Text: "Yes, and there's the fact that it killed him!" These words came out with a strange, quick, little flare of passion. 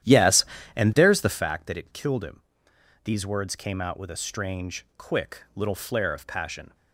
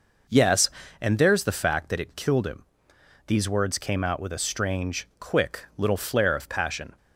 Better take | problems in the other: second | starts louder than the rest; strong; until 1.4 s; 11.5 dB

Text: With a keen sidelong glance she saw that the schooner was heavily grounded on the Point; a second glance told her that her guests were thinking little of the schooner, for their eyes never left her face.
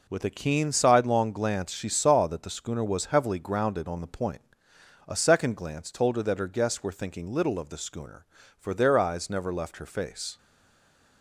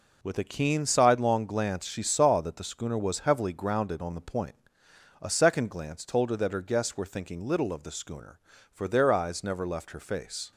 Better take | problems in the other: second | stays silent after the last word; slight; from 10.3 s on; 0.9 s long

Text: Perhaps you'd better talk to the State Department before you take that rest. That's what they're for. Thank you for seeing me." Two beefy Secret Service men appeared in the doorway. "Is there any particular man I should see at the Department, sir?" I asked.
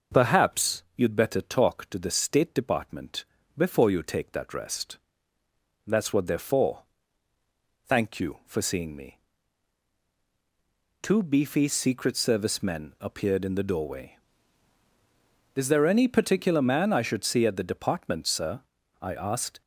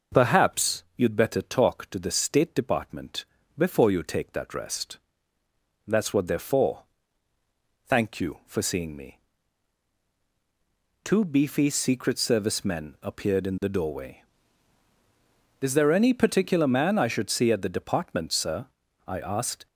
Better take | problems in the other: neither | pauses between "Department" and "before"; slight; the same in both

